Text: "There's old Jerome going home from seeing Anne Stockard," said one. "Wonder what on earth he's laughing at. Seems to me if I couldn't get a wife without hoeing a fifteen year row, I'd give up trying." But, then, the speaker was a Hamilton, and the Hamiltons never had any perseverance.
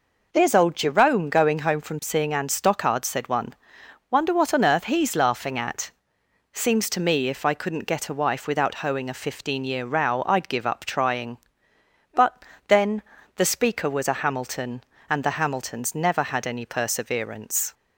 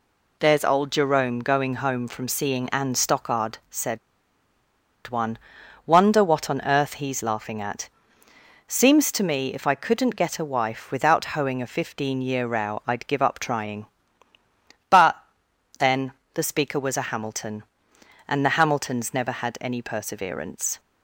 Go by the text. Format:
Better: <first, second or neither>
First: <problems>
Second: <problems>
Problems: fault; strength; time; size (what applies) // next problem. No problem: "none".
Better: first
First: none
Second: pauses between "said" and "one"; at 3.9 s; 1.0 s long